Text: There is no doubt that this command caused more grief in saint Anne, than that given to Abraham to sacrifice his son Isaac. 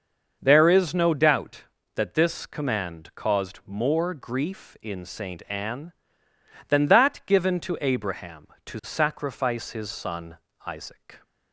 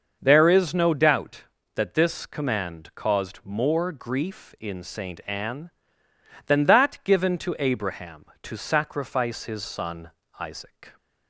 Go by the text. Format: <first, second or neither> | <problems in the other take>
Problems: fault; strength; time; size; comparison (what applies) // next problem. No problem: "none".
neither | starts louder than the rest; the same in both // pauses between "son" and "Isaac"; slight; the same in both